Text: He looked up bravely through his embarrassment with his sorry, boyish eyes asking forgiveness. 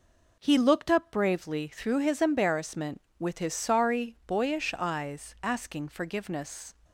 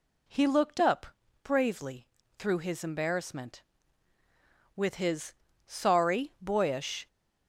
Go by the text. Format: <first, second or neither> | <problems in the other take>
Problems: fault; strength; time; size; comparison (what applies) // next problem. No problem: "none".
first | pauses between "up" and "bravely"; slight; at 1.0 s; 0.36 s long // pauses between "bravely" and "through"; slight; at 2.0 s; 0.32 s long // pauses between "his" and "sorry"; slight; at 5.3 s; 0.32 s long // stops before "eyes asking forgiveness"; at 7.0 s